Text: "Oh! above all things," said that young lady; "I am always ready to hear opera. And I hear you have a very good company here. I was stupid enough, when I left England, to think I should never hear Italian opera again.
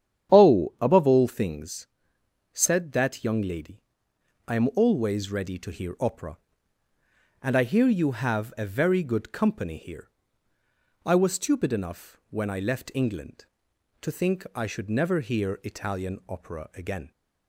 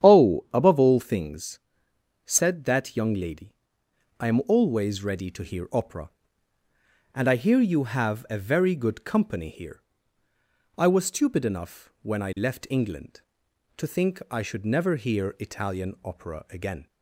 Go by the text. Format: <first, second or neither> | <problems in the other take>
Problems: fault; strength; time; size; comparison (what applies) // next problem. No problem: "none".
neither | starts louder than the rest; strong; the same in both